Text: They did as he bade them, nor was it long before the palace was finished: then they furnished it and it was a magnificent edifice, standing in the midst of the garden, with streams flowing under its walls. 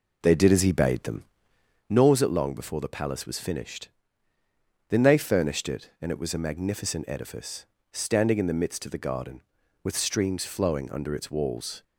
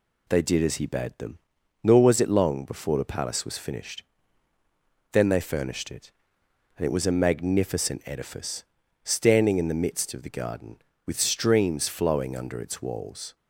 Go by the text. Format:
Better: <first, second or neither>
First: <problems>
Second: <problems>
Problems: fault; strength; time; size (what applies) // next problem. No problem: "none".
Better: second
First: starts louder than the rest; until 1.9 s; 4 dB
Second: none